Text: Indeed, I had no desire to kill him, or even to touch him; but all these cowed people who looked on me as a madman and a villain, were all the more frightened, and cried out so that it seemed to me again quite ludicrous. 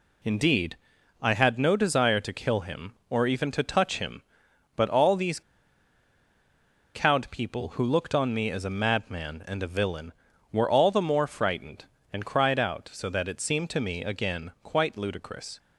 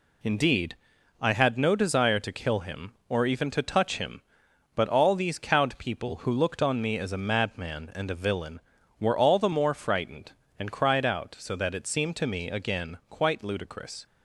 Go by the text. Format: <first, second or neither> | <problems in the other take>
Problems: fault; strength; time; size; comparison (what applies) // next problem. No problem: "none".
second | pauses between "these" and "cowed"; strong; at 5.4 s; 1.5 s long